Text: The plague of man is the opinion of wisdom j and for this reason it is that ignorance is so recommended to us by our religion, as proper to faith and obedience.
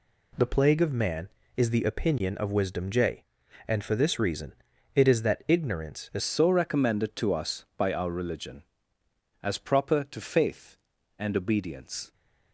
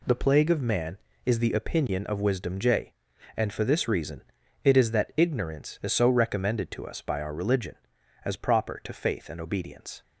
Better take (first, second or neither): second